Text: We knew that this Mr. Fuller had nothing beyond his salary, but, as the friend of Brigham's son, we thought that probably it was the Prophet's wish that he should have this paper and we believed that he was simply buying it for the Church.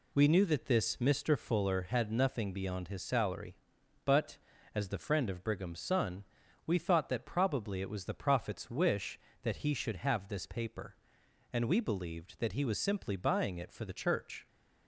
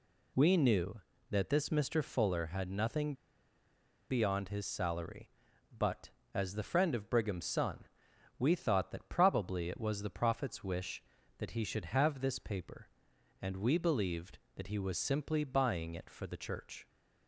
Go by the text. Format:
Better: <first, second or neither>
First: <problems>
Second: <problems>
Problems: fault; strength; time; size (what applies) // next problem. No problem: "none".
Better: first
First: none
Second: pauses between "nothing" and "beyond"; noticeable; at 3.1 s; 0.96 s long